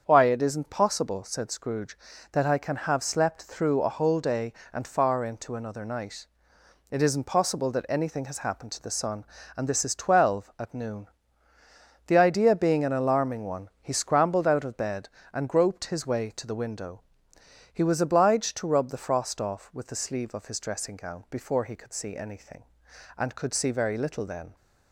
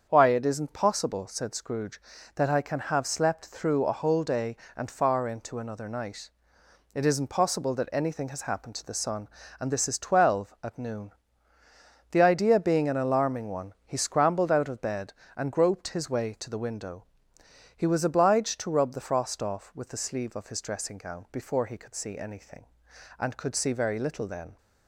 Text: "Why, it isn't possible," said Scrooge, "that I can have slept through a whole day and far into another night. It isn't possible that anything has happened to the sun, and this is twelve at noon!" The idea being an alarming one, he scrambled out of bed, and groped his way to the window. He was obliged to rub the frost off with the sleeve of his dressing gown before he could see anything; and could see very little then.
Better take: neither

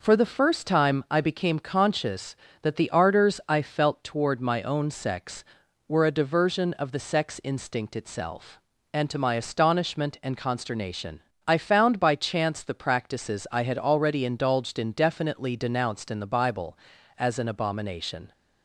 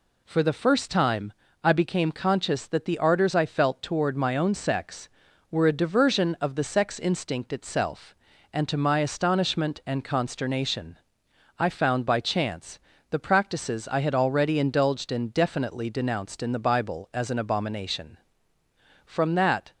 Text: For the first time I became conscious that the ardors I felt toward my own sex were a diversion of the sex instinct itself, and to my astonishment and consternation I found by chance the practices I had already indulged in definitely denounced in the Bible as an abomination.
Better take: first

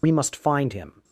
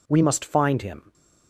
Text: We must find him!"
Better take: second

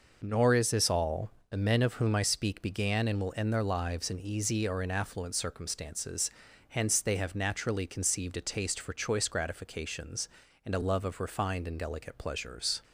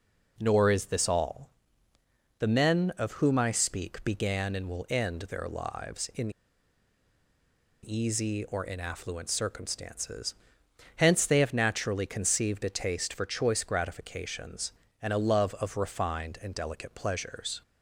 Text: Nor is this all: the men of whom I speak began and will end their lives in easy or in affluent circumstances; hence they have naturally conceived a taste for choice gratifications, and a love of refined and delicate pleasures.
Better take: first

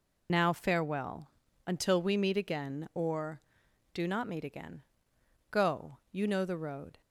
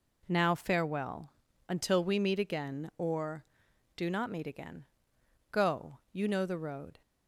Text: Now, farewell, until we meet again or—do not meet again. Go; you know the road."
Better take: second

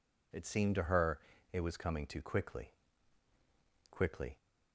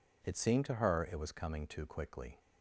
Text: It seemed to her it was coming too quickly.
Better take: second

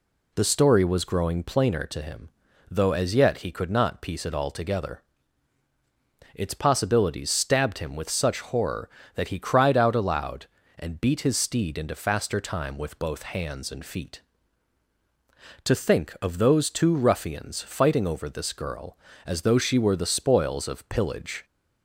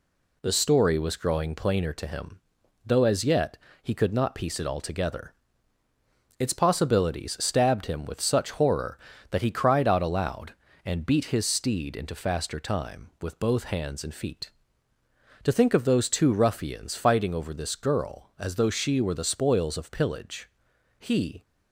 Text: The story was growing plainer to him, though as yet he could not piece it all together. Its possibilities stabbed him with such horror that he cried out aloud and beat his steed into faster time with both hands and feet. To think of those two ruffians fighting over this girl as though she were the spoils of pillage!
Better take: first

